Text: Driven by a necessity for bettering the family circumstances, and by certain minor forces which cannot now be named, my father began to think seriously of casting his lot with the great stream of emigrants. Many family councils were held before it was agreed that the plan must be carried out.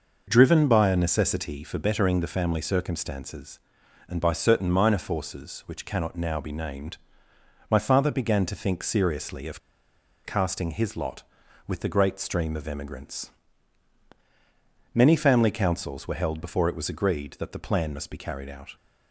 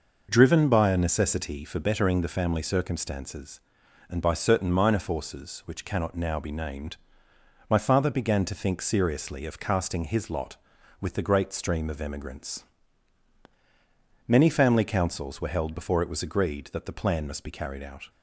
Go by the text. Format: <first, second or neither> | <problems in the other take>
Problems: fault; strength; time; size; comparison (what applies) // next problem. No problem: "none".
second | pauses between "of" and "casting"; noticeable; at 9.5 s; 0.67 s long